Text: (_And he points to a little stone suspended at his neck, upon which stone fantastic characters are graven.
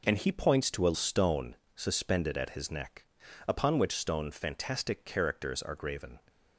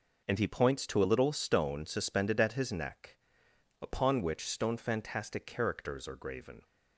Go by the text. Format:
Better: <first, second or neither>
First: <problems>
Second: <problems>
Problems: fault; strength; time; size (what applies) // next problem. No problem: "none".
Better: second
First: skips "little"; at 0.9 s // pauses between "stone" and "suspended"; slight; at 1.5 s; 0.18 s long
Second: none